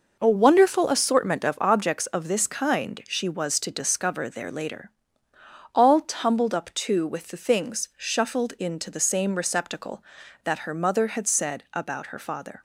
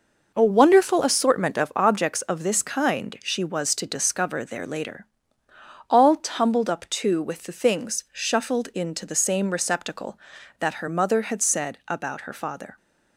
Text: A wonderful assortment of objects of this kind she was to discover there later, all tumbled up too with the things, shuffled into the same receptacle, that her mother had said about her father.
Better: neither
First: none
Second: none

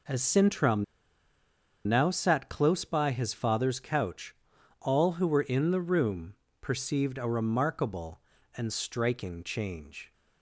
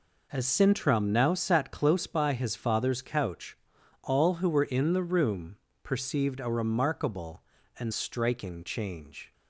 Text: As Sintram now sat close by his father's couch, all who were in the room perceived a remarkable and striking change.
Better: second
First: pauses between "Sintram" and "now"; at 0.8 s; 1.0 s long // pauses between "room" and "perceived"; slight; at 6.3 s; 0.26 s long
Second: pauses between "room" and "perceived"; slight; at 5.5 s; 0.26 s long

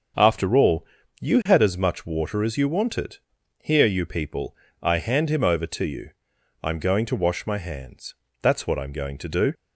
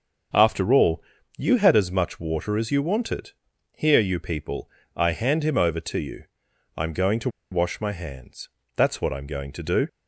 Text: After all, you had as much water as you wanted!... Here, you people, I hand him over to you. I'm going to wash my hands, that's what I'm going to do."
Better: first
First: starts louder than the rest; until 1.5 s; 6.5 dB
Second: starts louder than the rest; until 1.7 s; 6.5 dB // pauses between "to" and "wash"; slight; at 7.2 s; 0.22 s long

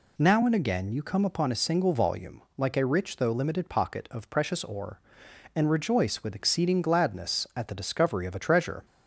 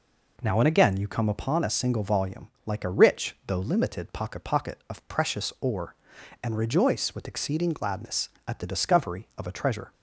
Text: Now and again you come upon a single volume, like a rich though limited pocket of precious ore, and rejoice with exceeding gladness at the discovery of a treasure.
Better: first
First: none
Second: says "pocket" twice; at 4.4 s

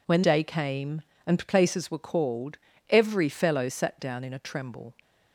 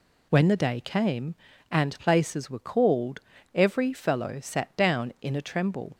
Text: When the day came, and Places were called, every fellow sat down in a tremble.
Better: second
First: skips "the"; at 0.2 s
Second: none

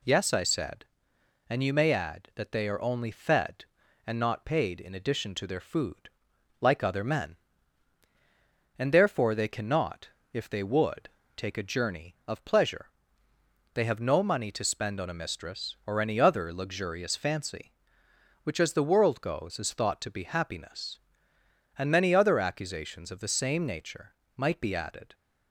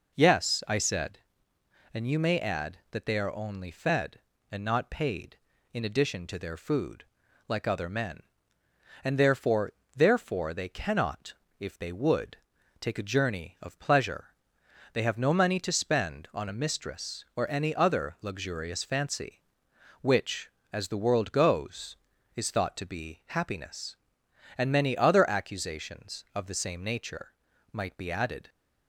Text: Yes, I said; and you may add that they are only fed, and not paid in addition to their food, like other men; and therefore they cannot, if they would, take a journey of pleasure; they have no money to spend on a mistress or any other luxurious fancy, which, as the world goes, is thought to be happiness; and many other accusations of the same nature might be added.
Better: first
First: pauses between "nature" and "might"; slight; at 24.1 s; 0.22 s long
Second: says "therefore" twice; at 9.9 s // pauses between "nature" and "might"; at 27.3 s; 0.42 s long

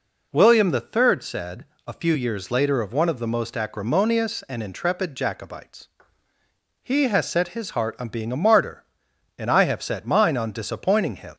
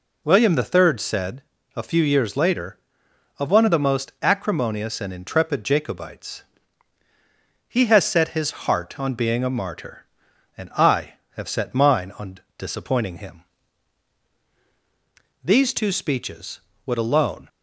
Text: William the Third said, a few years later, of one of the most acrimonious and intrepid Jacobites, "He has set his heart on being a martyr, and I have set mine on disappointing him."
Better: first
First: none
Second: pauses between "on" and "disappointing"; slight; at 12.3 s; 0.20 s long // goes on to say "These two speeches would alone"; strong; from 15.4 s on; 2.0 s long

